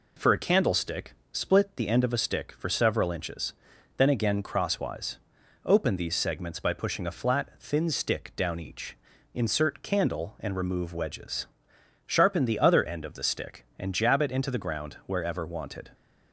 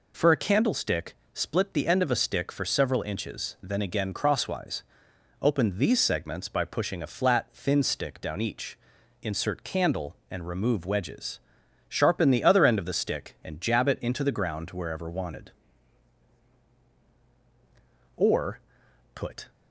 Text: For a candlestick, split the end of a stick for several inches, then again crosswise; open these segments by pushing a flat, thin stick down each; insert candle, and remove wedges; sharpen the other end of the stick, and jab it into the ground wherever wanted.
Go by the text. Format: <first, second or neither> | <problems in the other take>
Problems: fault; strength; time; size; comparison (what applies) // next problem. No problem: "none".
first | goes on to say "Or put"; from 18.1 s on; 1.3 s long